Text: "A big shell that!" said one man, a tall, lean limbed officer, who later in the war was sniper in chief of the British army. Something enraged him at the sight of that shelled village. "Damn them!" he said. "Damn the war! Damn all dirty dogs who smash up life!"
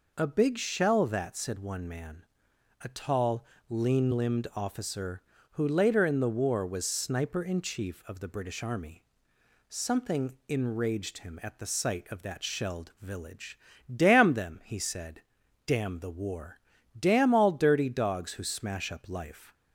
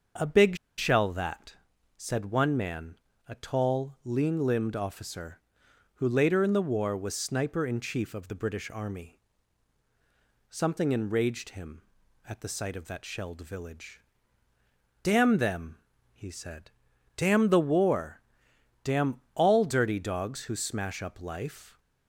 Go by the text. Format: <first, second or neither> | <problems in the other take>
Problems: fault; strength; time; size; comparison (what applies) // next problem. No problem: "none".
first | starts louder than the rest; until 1.4 s; 6.5 dB // pauses between "big" and "shell"; slight; at 0.5 s; 0.21 s long